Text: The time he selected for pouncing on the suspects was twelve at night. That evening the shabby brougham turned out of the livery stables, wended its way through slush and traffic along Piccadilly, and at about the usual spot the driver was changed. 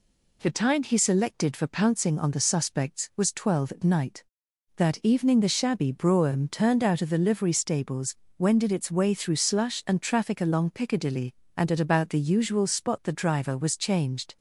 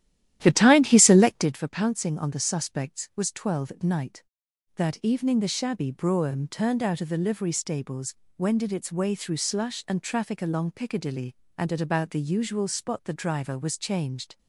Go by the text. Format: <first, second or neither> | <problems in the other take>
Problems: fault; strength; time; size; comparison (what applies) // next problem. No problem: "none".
first | starts louder than the rest; strong; until 1.6 s; 12.5 dB